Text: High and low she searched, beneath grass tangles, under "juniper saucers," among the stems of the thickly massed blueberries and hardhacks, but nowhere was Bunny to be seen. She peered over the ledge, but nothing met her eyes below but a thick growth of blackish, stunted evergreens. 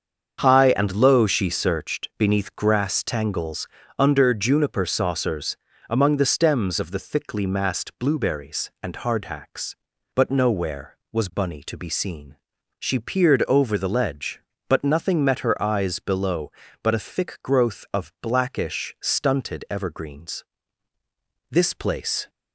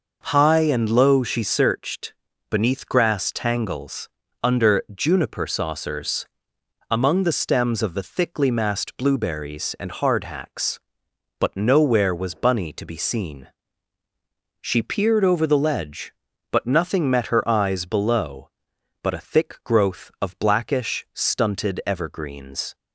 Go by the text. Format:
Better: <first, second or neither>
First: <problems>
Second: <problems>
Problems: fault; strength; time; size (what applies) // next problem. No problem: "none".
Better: second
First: starts louder than the rest; until 1.4 s; 7 dB // goes on to say "This place"; noticeable; from 21.5 s on; 0.78 s long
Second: none